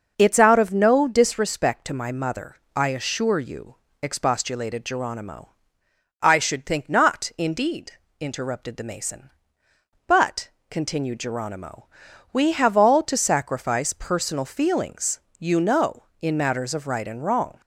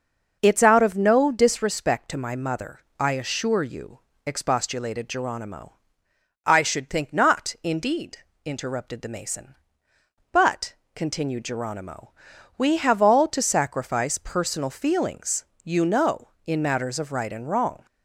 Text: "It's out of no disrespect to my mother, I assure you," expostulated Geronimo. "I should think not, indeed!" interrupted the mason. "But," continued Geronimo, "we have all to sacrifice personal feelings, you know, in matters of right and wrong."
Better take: neither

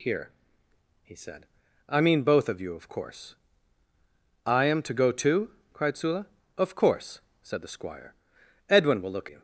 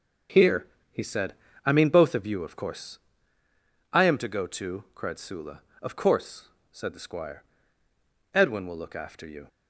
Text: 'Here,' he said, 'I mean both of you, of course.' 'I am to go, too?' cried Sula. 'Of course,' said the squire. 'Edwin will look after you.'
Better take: second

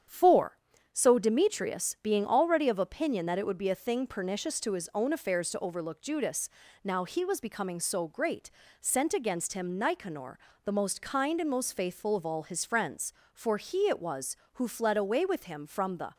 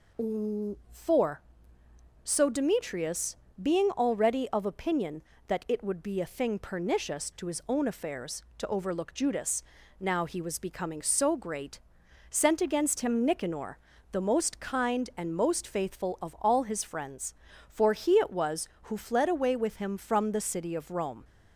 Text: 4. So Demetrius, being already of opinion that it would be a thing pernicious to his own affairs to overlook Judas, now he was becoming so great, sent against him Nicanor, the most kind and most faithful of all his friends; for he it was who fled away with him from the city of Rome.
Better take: second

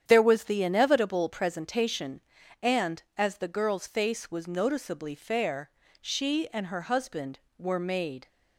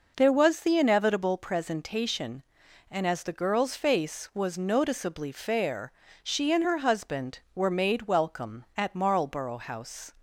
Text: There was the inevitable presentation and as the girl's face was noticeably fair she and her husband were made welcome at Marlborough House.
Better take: second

